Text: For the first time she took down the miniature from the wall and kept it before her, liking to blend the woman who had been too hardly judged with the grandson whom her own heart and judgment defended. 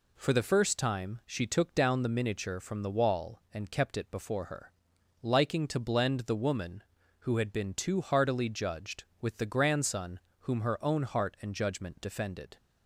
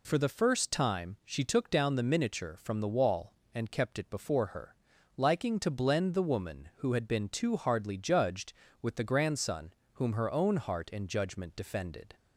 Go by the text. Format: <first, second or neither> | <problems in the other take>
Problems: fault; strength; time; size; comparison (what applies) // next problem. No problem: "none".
second | says "heartily" for "hardly"; at 8.0 s // pauses between "grandson" and "whom"; slight; at 10.1 s; 0.22 s long; slight in the second